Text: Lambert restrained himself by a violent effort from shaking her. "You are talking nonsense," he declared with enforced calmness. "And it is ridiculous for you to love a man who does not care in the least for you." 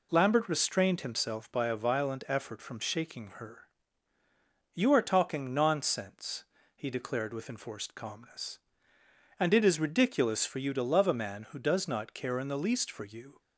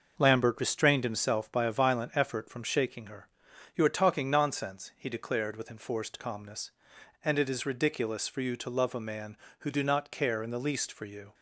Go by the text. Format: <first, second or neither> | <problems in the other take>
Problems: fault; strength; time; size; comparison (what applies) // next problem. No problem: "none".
first | says "do" for "does"; at 9.6 s